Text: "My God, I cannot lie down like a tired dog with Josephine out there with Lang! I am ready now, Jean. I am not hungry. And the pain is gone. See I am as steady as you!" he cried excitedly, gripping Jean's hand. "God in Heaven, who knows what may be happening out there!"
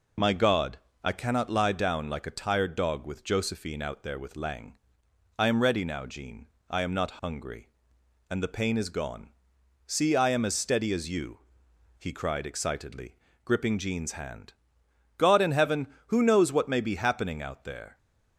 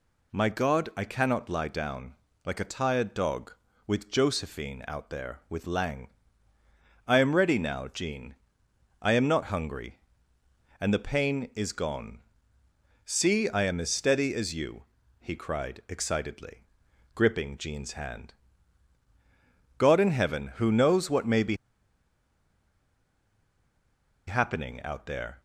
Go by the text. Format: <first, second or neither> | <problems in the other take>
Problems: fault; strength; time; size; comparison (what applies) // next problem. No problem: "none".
first | pauses between "down" and "like"; slight; at 2.1 s; 0.32 s long // pauses between "be" and "happening"; strong; at 21.5 s; 2.7 s long